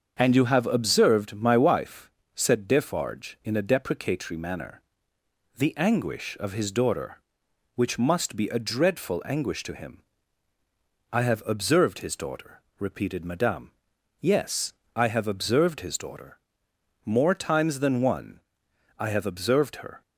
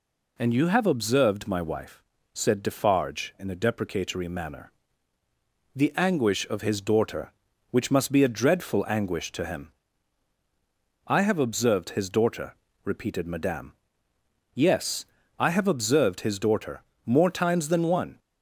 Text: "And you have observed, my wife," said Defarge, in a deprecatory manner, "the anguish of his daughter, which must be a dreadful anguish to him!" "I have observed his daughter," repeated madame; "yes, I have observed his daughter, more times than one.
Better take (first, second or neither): second